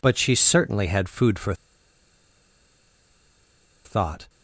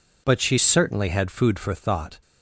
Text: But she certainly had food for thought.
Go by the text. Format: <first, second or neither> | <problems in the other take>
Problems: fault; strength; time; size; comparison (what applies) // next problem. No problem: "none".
second | pauses between "for" and "thought"; strong; at 1.5 s; 2.3 s long